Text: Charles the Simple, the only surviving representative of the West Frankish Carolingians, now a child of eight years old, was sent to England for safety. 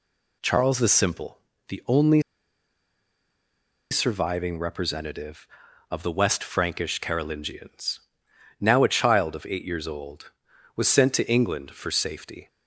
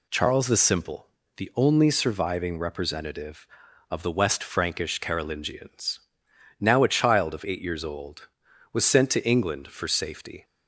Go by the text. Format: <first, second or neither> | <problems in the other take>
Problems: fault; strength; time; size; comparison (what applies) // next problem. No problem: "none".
second | pauses between "only" and "surviving"; strong; at 2.2 s; 1.7 s long